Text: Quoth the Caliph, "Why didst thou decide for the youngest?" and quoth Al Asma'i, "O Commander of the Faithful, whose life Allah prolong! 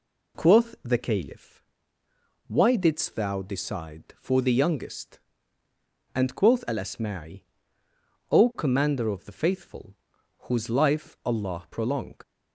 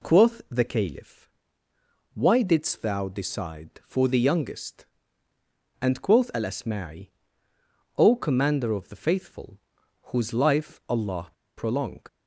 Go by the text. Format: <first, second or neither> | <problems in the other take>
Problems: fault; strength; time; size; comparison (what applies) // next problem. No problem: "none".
first | pauses between "Allah" and "prolong"; slight; at 11.3 s; 0.26 s long